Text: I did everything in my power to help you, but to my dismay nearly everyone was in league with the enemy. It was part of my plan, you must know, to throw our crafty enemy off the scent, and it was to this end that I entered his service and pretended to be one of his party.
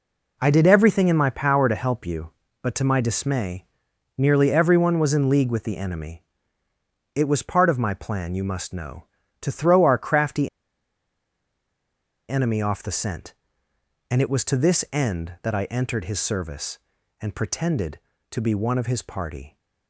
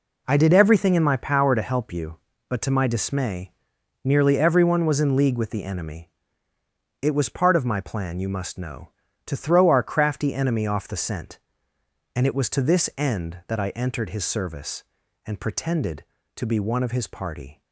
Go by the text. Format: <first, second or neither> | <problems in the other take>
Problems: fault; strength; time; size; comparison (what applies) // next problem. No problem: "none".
second | pauses between "dismay" and "nearly"; noticeable; at 3.6 s; 0.56 s long; noticeable in the second // pauses between "crafty" and "enemy"; strong; at 10.4 s; 1.8 s long